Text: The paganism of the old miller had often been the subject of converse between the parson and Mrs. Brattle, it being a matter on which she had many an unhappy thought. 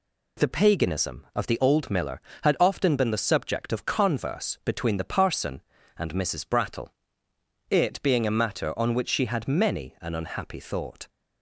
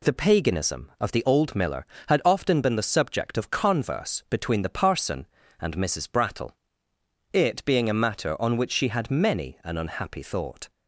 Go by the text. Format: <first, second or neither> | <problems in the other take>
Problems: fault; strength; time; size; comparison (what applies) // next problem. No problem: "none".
neither | none